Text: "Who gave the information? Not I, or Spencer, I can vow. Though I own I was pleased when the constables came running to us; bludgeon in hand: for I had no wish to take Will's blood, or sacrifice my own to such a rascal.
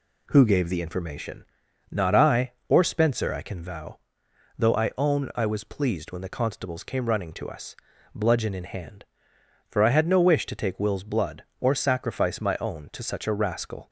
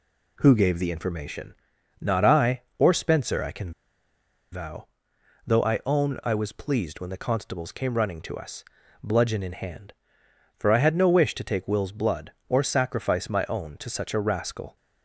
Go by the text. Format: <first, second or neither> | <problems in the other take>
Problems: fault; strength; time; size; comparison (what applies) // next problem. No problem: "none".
first | pauses between "can" and "vow"; noticeable; at 3.7 s; 0.81 s long